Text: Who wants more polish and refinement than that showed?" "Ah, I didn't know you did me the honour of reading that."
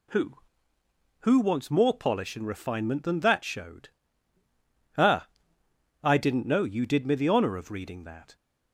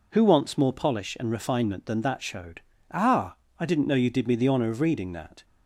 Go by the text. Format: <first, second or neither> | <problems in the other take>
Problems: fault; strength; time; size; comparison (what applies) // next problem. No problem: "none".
second | says "Who" twice; at 1.1 s